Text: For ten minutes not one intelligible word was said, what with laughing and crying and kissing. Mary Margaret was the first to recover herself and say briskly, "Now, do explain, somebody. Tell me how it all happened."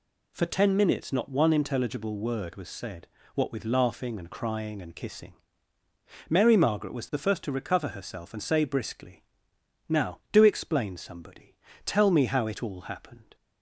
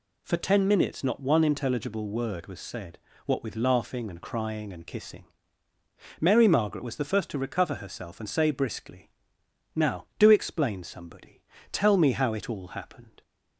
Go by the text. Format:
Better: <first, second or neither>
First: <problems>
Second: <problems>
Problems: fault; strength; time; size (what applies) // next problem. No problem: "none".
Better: neither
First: none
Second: none